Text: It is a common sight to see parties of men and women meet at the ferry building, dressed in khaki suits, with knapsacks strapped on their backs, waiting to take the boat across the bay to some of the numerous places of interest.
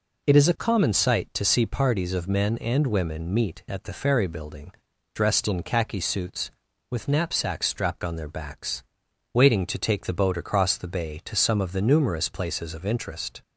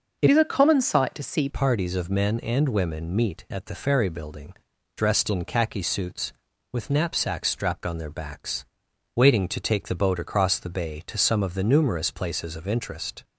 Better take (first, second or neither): first